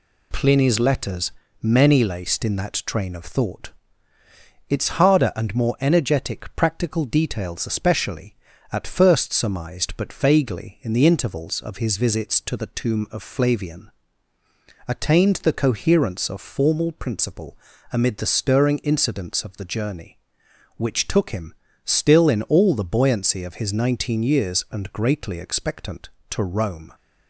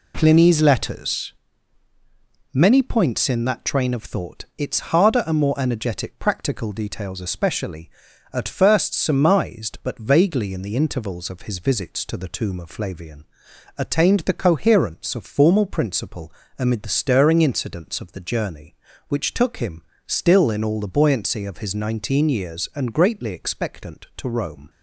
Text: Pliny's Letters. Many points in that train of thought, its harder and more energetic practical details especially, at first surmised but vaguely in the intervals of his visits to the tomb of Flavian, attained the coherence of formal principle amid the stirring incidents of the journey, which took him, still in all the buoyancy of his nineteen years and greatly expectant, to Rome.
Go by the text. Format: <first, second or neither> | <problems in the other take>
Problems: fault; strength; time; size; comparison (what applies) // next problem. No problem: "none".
second | says "laced" for "points"; at 2.0 s // pauses between "principle" and "amid"; slight; at 17.5 s; 0.36 s long; slight in the second